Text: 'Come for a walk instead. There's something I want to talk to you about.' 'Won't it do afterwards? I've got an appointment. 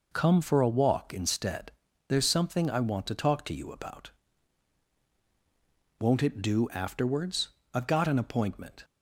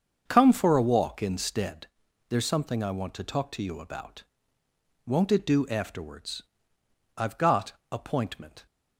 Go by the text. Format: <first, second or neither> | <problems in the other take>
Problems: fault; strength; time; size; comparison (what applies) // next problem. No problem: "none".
first | starts louder than the rest; until 1.2 s; 7 dB // skips "an"; at 7.8 s